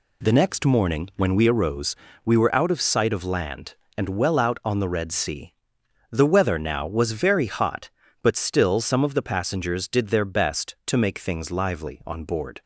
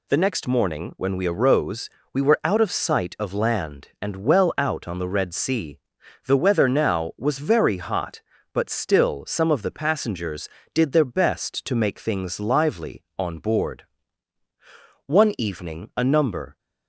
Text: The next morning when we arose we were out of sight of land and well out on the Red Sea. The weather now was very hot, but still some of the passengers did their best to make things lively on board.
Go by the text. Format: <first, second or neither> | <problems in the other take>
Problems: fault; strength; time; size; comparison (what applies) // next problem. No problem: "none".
first | pauses between "arose" and "we"; slight; at 1.8 s; 0.24 s long; slight in the first // goes on to say "One evening a number"; from 15.0 s on; 1.5 s long